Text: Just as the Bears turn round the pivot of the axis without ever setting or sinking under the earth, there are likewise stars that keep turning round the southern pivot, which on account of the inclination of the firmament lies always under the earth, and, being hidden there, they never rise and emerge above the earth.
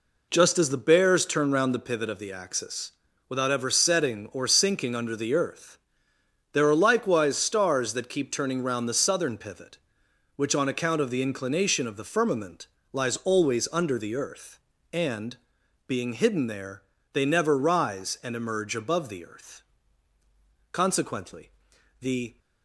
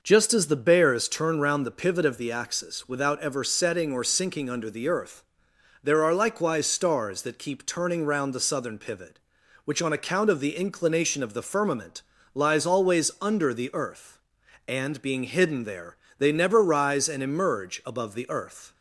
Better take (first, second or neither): second